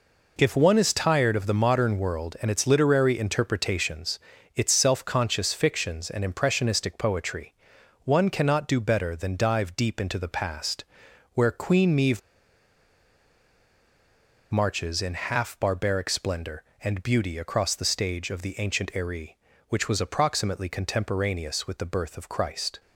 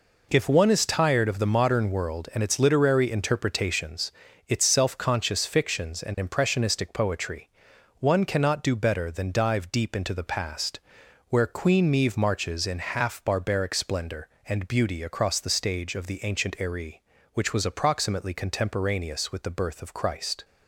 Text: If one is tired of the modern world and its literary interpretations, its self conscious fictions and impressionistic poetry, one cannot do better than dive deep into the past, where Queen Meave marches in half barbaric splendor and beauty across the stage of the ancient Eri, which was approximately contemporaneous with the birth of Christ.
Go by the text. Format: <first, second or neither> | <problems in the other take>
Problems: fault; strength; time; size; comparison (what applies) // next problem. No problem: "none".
second | pauses between "Meave" and "marches"; strong; at 12.2 s; 2.3 s long